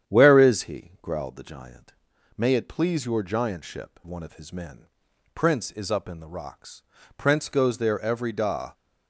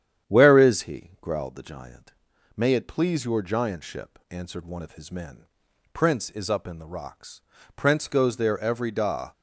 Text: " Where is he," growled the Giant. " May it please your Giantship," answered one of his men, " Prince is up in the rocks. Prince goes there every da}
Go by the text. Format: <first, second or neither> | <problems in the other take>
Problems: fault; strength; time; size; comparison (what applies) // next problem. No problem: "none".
second | starts louder than the rest; strong; until 1.1 s; 9.5 dB; strong in the second // skips "answered"; at 4.0 s